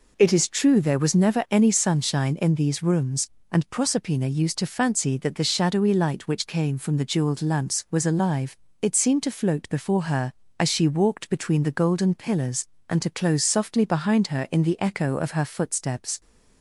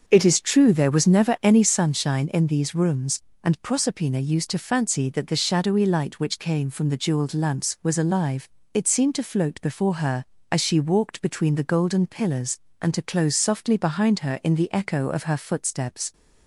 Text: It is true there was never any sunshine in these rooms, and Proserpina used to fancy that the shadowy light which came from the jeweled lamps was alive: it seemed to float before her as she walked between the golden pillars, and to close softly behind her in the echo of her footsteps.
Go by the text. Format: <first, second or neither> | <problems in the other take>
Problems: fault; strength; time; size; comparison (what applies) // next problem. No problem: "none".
first | starts louder than the rest; until 1.9 s; 6.5 dB